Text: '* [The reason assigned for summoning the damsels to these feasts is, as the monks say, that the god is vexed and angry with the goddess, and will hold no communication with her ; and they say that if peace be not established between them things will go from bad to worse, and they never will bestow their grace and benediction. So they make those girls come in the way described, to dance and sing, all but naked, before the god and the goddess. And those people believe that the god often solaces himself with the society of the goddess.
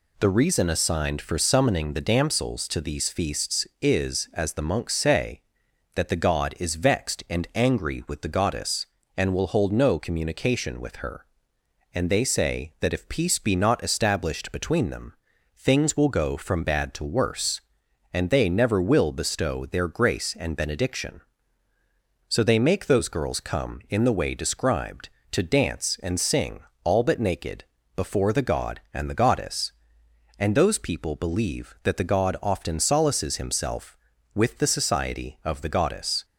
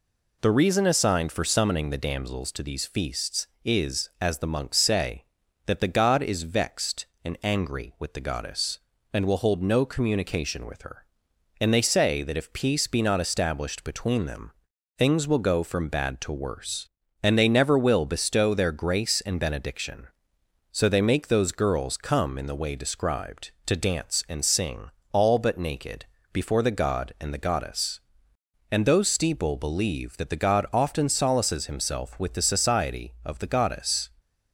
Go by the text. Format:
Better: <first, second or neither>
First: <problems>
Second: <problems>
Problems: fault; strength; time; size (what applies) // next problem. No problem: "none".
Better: first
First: pauses between "them" and "things"; at 15.1 s; 0.44 s long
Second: pauses between "them" and "things"; noticeable; at 14.5 s; 0.46 s long // says "steeple" for "people"; at 29.0 s